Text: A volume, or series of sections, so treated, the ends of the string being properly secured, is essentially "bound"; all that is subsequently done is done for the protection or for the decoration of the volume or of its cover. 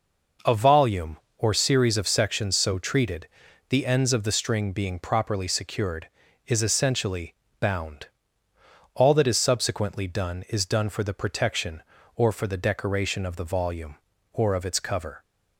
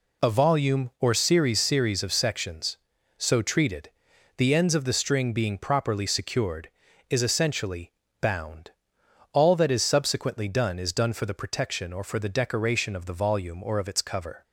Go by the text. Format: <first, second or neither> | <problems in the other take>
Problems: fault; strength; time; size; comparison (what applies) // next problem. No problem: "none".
first | says "series" twice; at 1.6 s // pauses between "essentially" and "bound"; slight; at 7.9 s; 0.28 s long; slight in the first